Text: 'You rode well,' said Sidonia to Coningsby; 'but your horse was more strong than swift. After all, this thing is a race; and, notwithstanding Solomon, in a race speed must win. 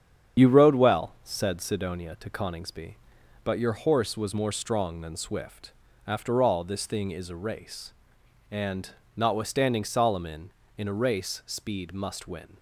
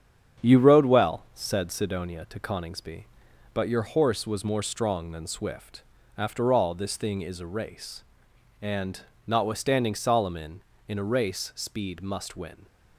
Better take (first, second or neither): second